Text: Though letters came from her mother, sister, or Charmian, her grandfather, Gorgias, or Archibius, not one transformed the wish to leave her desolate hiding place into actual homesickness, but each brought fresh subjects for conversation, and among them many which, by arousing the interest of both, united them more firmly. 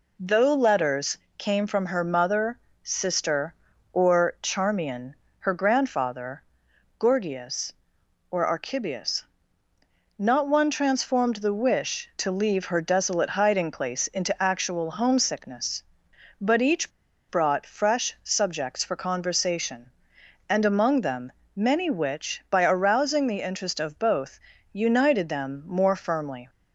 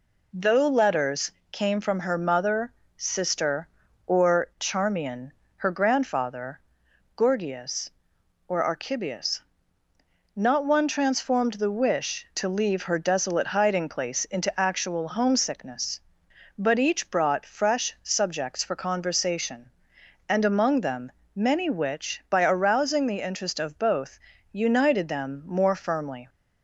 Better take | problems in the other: second | pauses between "letters" and "came"; slight; at 1.1 s; 0.22 s long; slight in the second // pauses between "each" and "brought"; at 16.9 s; 0.39 s long // pauses between "them" and "many"; slight; at 21.3 s; 0.24 s long; slight in the second

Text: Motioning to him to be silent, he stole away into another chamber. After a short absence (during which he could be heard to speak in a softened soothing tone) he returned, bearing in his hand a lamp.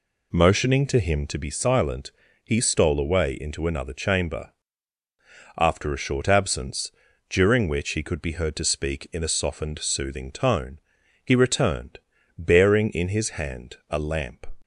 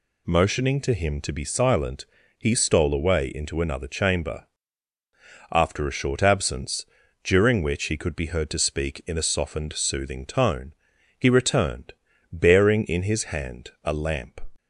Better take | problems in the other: second | starts louder than the rest; slight; until 1.4 s; 2.5 dB

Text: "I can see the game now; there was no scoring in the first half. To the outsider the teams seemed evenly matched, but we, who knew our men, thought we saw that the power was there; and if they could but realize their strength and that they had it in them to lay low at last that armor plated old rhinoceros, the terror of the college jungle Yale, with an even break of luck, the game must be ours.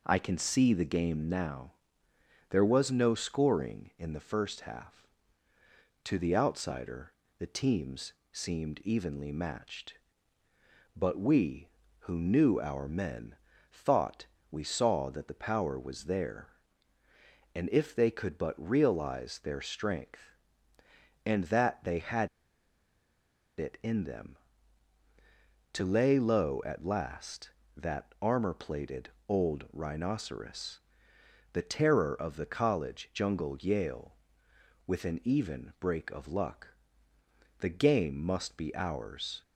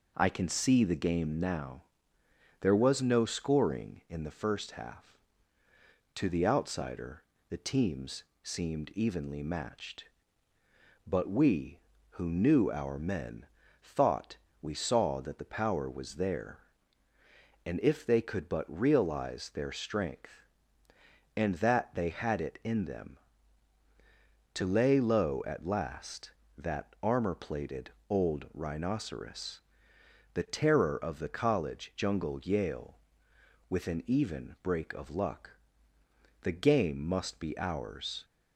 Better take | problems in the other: second | pauses between "outsider" and "the"; slight; at 7.1 s; 0.26 s long; slight in the second // pauses between "teams" and "seemed"; slight; at 8.1 s; 0.20 s long; slight in the second // pauses between "thought" and "we"; slight; at 14.2 s; 0.24 s long; slight in the second // pauses between "had" and "it"; strong; at 22.2 s; 1.2 s long // pauses between "plated" and "old"; slight; at 29.0 s; 0.18 s long; slight in the second

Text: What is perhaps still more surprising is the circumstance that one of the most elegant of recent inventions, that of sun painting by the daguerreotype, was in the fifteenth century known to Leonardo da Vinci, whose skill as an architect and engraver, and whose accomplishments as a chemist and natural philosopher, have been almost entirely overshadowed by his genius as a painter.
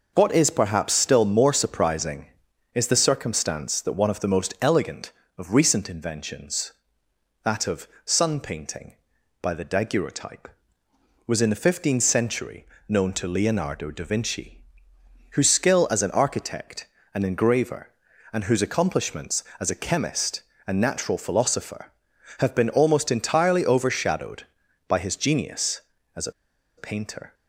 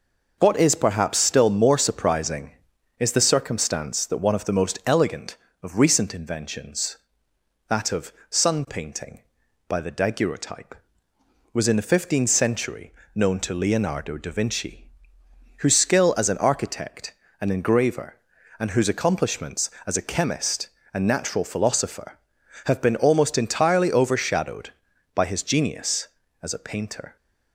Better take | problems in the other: second | pauses between "of" and "sun"; slight; at 7.8 s; 0.18 s long; slight in the second // pauses between "century" and "known"; slight; at 12.6 s; 0.20 s long; slight in the second // pauses between "a" and "painter"; noticeable; at 26.3 s; 0.46 s long

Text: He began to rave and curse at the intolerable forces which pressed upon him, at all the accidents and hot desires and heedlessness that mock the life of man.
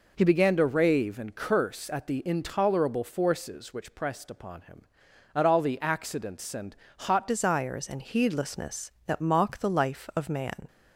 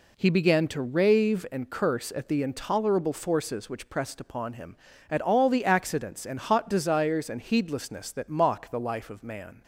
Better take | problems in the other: second | pauses between "and" and "hot"; slight; at 6.7 s; 0.26 s long // changes voice at "desires"; from 7.2 s on; 3.4 s long

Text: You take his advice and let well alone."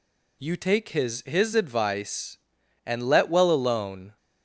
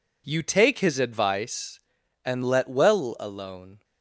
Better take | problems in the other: second | says "his" twice; at 1.2 s

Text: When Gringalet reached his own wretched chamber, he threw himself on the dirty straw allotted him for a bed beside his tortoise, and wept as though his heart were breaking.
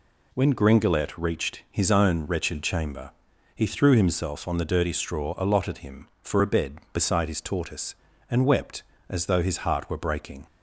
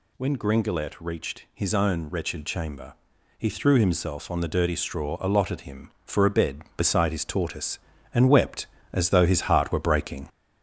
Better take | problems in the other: first | gets louder; noticeable; throughout; 4.5 dB

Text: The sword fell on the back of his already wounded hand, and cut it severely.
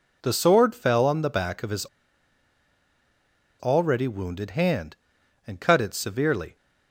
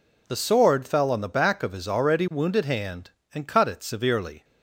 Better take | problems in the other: second | pauses between "his" and "already"; strong; at 1.8 s; 1.7 s long

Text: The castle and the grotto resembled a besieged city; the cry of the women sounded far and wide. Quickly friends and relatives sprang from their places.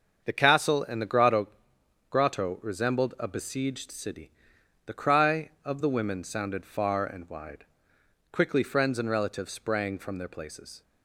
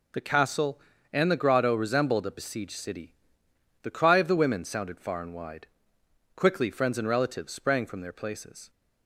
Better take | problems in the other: second | starts louder than the rest; until 1.2 s; 6.5 dB // says "grotto" twice; at 2.1 s

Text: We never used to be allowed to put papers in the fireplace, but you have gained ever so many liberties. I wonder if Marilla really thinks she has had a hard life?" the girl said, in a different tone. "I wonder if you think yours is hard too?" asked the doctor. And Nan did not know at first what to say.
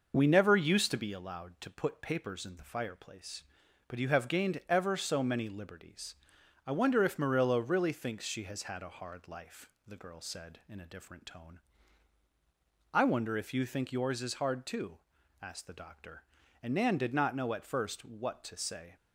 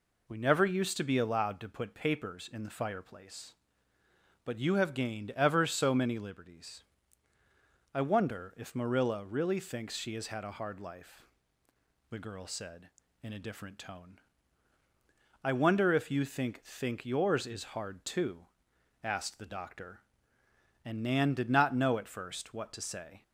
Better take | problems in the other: first | says "think" twice; at 16.6 s

